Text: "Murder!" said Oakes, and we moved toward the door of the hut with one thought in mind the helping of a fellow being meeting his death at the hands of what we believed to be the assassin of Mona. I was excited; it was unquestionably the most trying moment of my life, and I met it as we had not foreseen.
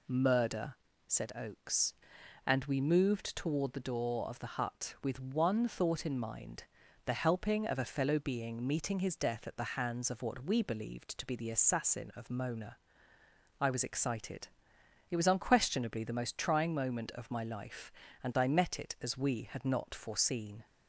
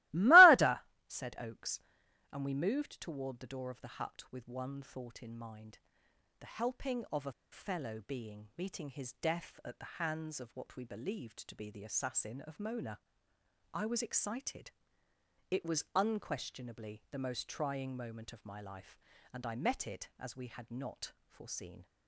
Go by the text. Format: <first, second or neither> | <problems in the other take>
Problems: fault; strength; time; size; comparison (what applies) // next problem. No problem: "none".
first | starts louder than the rest; strong; until 1.4 s; 19.5 dB // pauses between "mind" and "the"; noticeable; at 5.7 s; 0.62 s long; also in the first // pauses between "a" and "fellow"; slight; at 7.3 s; 0.19 s long